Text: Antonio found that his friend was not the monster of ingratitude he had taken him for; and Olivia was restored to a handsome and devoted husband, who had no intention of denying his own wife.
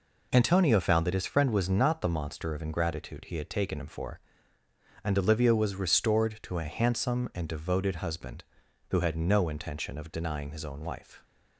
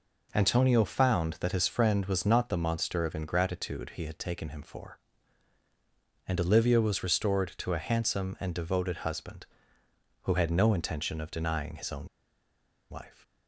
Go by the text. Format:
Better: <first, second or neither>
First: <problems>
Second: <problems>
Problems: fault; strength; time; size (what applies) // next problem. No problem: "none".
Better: first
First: none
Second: pauses between "own" and "wife"; noticeable; at 12.0 s; 0.84 s long